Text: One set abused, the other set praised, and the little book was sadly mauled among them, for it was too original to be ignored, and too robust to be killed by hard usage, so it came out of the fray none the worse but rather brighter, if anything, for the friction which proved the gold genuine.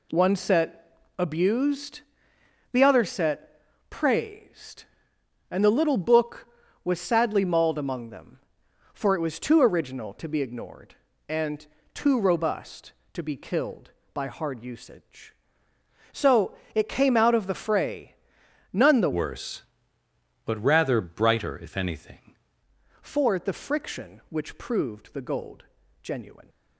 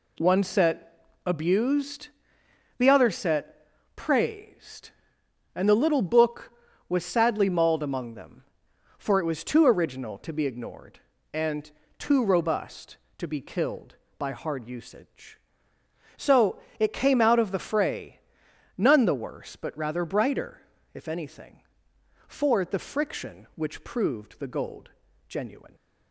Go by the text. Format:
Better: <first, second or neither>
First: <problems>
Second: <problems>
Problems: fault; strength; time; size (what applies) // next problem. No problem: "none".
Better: second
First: pauses between "set" and "abused"; slight; at 0.9 s; 0.26 s long // pauses between "set" and "praised"; slight; at 3.6 s; 0.30 s long // pauses between "and" and "too"; slight; at 11.6 s; 0.28 s long // pauses between "so" and "it"; slight; at 16.5 s; 0.20 s long // pauses between "fray" and "none"; noticeable; at 18.1 s; 0.58 s long // changes voice from "worse" to "anything"; from 19.1 to 22.3 s; 3.2 s long // pauses between "gold" and "genuine"; slight; at 25.6 s; 0.36 s long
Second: pauses between "set" and "abused"; slight; at 0.9 s; 0.26 s long // pauses between "set" and "praised"; slight; at 3.6 s; 0.30 s long // pauses between "and" and "too"; slight; at 11.7 s; 0.28 s long // pauses between "so" and "it"; slight; at 16.5 s; 0.20 s long // pauses between "fray" and "none"; noticeable; at 18.1 s; 0.58 s long // pauses between "gold" and "genuine"; slight; at 24.9 s; 0.36 s long